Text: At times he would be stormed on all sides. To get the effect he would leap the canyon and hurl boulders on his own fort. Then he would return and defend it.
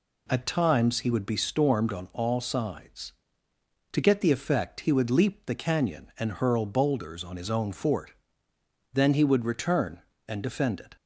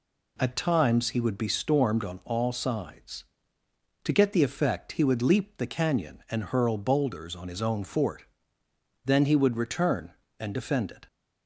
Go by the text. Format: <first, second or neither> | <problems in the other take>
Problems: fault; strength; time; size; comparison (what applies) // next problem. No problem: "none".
neither | none